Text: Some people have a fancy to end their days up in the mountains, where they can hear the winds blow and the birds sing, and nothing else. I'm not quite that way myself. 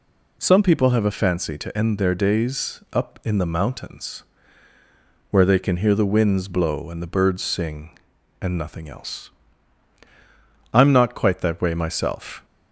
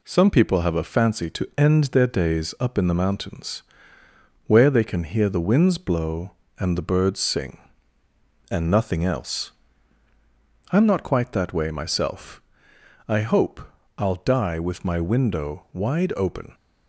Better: first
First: none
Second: goes on to say "I hope I'll die with my window wide open"; strong; from 13.0 s on; 3.4 s long

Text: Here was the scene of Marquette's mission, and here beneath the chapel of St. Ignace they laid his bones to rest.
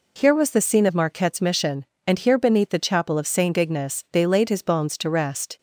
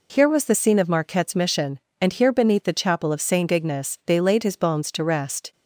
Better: neither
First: none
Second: none

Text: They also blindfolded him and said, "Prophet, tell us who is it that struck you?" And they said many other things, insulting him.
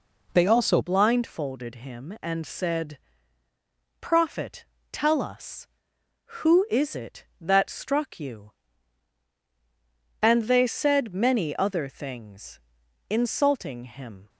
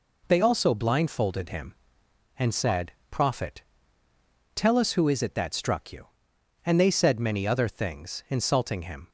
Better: second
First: changes voice at "blindfolded"; from 0.8 s on; 13.4 s long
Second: none

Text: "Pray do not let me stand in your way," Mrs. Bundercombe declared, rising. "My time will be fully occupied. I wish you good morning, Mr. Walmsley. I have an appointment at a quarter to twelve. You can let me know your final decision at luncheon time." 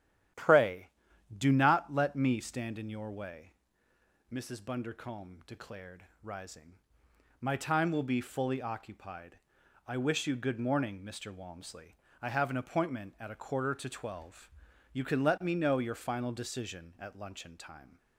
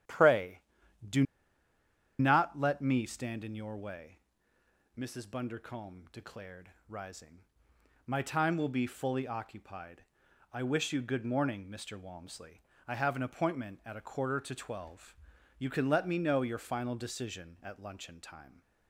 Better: first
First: starts louder than the rest; strong; until 1.8 s; 11 dB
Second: starts louder than the rest; strong; until 2.5 s; 11 dB // pauses between "do" and "not"; noticeable; at 1.2 s; 0.97 s long

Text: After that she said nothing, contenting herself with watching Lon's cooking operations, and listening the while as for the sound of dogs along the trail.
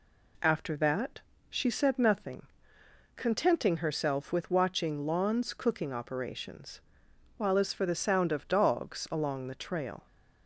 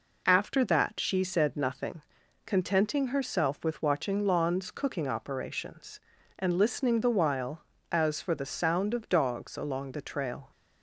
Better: second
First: pauses between "that" and "she"; slight; at 1.1 s; 0.28 s long // skips "and listening the"; at 7.0 s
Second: none

